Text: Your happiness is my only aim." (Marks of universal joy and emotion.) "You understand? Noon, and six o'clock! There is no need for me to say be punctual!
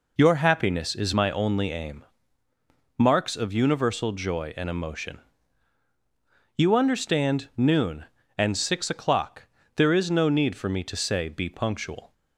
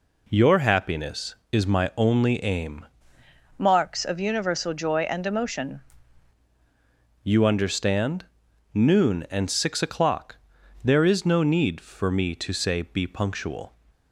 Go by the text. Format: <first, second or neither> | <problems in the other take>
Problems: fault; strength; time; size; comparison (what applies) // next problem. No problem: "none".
first | changes voice from "Marks" to "emotion"; from 3.5 to 5.8 s; 2.3 s long